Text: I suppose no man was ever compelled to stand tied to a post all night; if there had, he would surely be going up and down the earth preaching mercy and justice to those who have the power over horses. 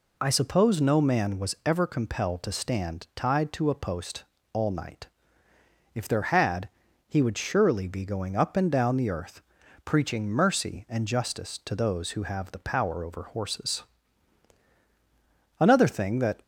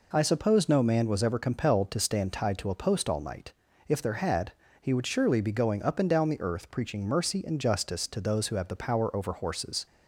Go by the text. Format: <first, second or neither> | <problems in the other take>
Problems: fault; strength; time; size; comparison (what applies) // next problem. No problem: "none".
second | pauses between "post" and "all"; slight; at 4.2 s; 0.28 s long // pauses between "earth" and "preaching"; at 9.4 s; 0.44 s long // goes on to say "Another thing that"; noticeable; from 15.5 s on; 0.82 s long